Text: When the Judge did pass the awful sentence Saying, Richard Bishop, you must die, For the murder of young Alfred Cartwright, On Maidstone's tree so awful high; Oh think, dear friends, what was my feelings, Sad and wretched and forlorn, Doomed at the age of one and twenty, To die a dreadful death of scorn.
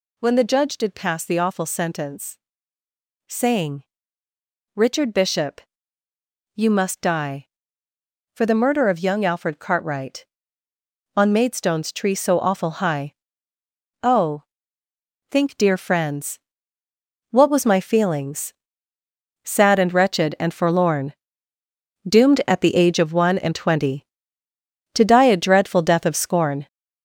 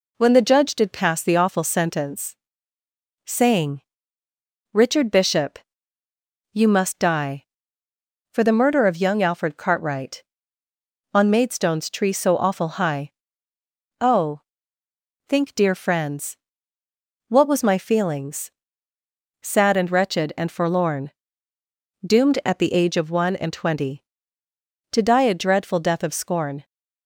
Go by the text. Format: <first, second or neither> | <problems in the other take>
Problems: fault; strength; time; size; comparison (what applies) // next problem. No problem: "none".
second | gets louder; throughout; 7 dB // pauses between "sentence" and "Saying"; noticeable; at 2.3 s; 0.88 s long; noticeable in the second // pauses between "Oh" and "think"; noticeable; at 14.4 s; 0.86 s long; noticeable in the second